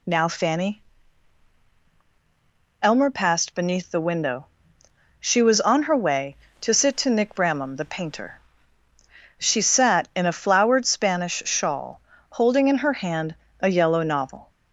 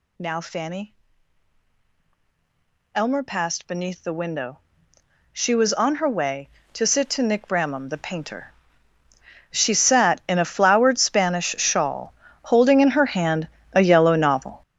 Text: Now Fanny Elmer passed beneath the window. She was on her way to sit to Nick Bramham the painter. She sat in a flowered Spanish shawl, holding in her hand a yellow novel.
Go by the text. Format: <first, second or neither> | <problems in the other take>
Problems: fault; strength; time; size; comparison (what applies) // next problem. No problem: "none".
first | gets louder; strong; throughout; 12 dB // pauses between "Fanny" and "Elmer"; strong; at 0.9 s; 1.9 s long; strong in the first // pauses between "hand" and "a"; slight; at 13.4 s; 0.26 s long; slight in the first